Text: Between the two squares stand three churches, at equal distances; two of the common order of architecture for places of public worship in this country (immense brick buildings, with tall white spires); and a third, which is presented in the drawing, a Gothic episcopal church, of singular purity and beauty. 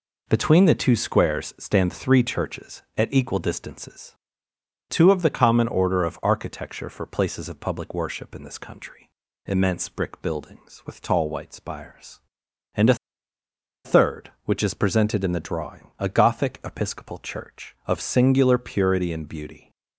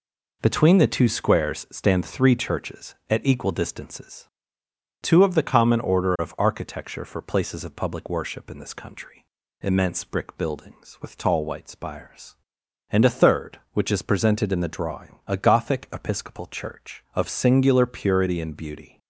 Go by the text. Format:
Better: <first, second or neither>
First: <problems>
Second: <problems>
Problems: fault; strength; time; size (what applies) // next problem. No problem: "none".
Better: second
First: pauses between "a" and "third"; noticeable; at 12.9 s; 0.90 s long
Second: none